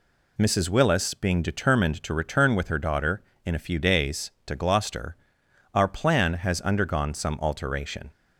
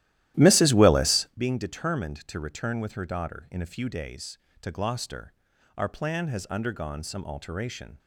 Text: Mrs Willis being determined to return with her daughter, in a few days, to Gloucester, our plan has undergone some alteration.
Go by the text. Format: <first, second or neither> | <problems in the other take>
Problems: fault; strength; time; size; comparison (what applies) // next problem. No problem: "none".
first | starts louder than the rest; strong; until 1.4 s; 14 dB